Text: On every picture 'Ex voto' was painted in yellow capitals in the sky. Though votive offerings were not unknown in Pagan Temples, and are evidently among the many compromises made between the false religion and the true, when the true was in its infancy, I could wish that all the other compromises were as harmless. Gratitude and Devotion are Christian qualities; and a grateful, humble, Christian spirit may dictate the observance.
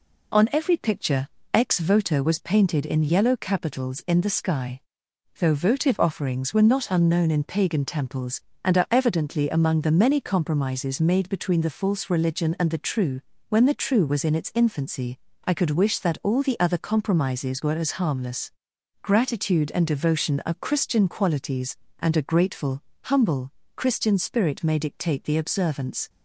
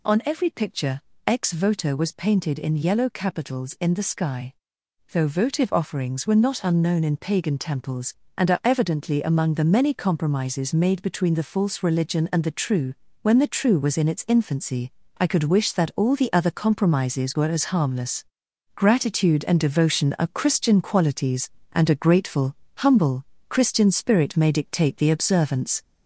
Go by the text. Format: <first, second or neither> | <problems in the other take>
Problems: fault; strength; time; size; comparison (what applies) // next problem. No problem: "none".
first | gets louder; slight; throughout; 3 dB // pauses between "picture" and "Ex"; slight; at 1.0 s; 0.26 s long; slight in the first